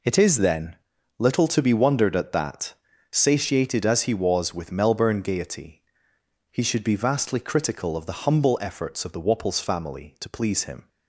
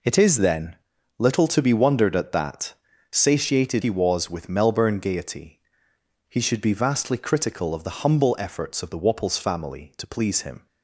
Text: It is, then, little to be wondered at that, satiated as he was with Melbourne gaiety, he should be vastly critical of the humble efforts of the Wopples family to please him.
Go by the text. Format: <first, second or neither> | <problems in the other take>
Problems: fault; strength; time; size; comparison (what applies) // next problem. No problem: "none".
first | skips "as"; at 3.8 s